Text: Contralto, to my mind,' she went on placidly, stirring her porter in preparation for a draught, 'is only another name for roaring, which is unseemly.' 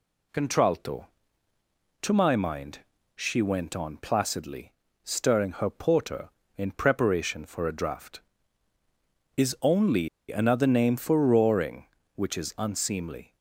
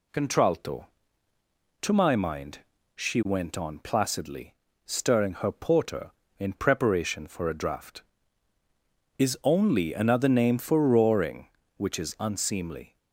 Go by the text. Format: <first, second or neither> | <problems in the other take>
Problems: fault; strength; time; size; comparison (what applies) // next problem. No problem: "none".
second | pauses between "only" and "another"; slight; at 10.0 s; 0.22 s long